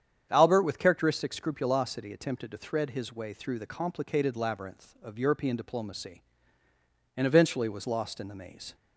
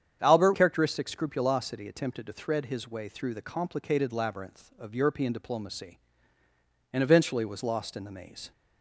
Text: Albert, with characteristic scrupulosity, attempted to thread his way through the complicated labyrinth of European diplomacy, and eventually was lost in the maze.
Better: first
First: starts louder than the rest; strong; until 1.3 s; 8.5 dB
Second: starts louder than the rest; strong; until 1.2 s; 8.5 dB // skips "with"; at 0.5 s

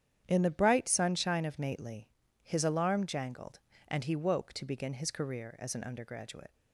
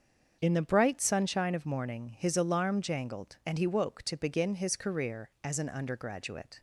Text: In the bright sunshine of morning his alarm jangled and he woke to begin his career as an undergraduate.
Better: second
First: starts louder than the rest; strong; until 1.2 s; 9.5 dB // says "nately" for "morning"; at 1.5 s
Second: starts louder than the rest; until 1.4 s; 7 dB

